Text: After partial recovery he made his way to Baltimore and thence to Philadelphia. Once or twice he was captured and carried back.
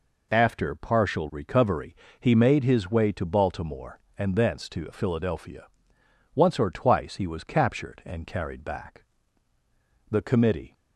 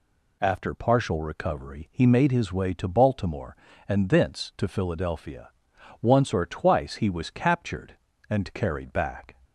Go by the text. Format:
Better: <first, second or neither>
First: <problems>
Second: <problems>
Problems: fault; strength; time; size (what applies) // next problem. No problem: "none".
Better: second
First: pauses between "recovery" and "he"; slight; at 1.9 s; 0.24 s long // goes on to say "The Committee"; noticeable; from 10.0 s on; 0.64 s long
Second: none